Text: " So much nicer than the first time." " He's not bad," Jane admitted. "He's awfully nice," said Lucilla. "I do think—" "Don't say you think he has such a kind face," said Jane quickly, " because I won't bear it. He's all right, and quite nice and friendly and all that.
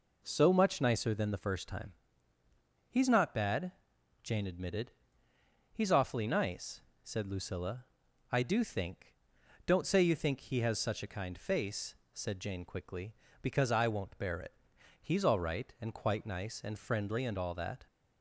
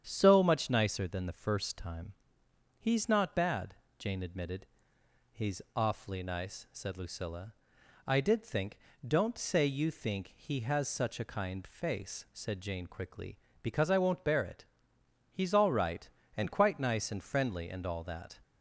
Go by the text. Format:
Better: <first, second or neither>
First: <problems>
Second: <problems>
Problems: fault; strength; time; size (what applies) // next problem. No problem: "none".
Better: first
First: none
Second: starts louder than the rest; strong; until 1.0 s; 8 dB // says "did" for "do"; at 8.1 s